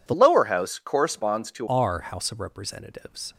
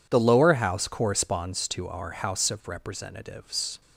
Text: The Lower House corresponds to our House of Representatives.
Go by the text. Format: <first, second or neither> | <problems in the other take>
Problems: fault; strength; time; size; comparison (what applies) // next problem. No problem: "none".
second | changes voice from "Lower" to "to"; from 0.1 to 1.6 s; 1.5 s long